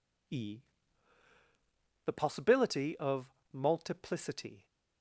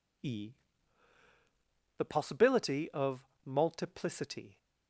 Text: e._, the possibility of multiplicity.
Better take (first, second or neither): neither